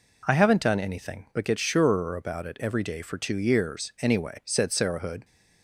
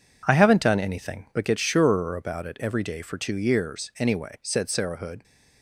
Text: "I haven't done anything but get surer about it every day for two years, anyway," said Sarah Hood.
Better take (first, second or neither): first